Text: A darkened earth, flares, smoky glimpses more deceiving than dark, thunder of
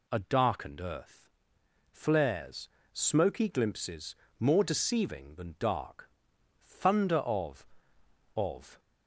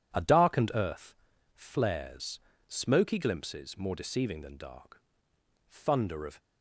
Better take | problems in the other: second | pauses between "glimpses" and "more"; slight; at 4.1 s; 0.24 s long // says "of" twice; at 8.3 s

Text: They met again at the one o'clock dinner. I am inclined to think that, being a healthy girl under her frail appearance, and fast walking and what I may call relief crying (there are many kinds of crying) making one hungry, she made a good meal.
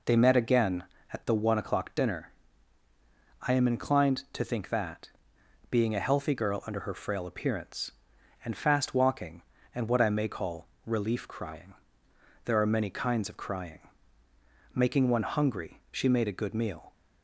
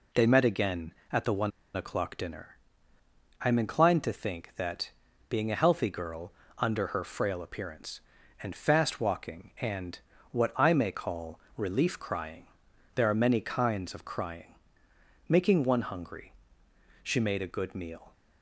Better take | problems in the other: first | pauses between "one" and "o'clock"; slight; at 1.5 s; 0.25 s long // pauses between "girl" and "under"; slight; at 6.3 s; 0.26 s long // pauses between "and" and "what"; slight; at 9.9 s; 0.34 s long // pauses between "call" and "relief"; slight; at 11.3 s; 0.16 s long; slight in the first

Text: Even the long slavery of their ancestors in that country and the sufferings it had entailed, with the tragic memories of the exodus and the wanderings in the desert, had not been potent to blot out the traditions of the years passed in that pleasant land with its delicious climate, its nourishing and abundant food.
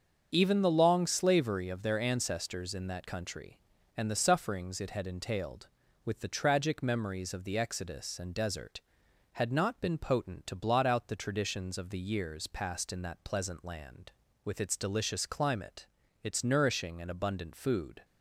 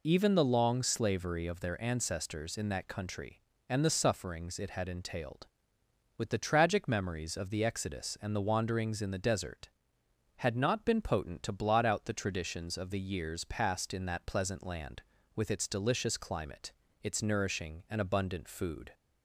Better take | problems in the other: second | starts louder than the rest; until 1.3 s; 7 dB // skips "the wanderings in the"; at 8.3 s

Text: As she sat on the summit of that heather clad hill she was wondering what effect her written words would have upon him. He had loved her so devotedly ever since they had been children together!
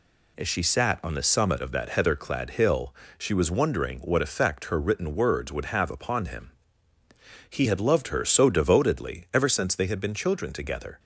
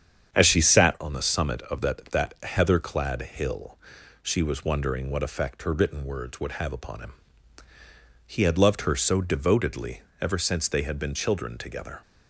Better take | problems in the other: first | starts louder than the rest; strong; until 1.3 s; 8 dB // says "that" twice; at 2.0 s // pauses between "hill" and "she"; noticeable; at 3.7 s; 0.46 s long; slight in the first // pauses between "devotedly" and "ever"; slight; at 10.0 s; 0.18 s long

